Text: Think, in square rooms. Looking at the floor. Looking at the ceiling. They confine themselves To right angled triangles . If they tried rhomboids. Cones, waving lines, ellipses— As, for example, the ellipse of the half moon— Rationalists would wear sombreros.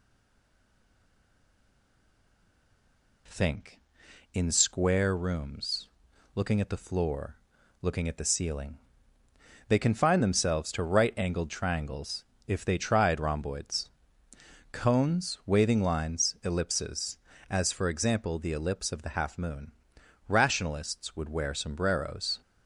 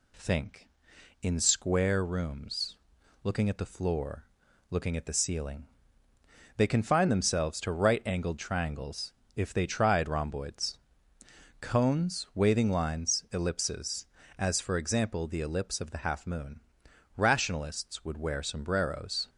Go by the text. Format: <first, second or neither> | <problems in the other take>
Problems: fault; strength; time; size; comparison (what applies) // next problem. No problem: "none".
second | stays silent before the first word; strong; until 3.2 s; 3.2 s long